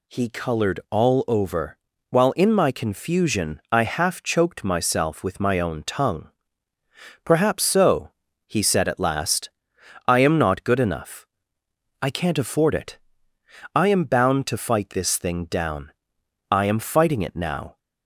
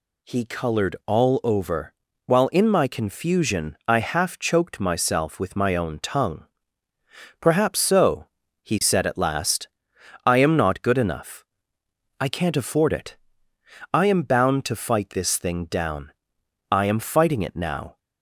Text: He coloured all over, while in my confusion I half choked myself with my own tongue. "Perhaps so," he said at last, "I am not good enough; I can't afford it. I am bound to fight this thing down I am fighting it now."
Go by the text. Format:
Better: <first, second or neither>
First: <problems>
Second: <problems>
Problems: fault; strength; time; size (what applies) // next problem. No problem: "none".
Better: neither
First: pauses between "down" and "I"; noticeable; at 15.9 s; 0.60 s long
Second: pauses between "down" and "I"; noticeable; at 16.1 s; 0.60 s long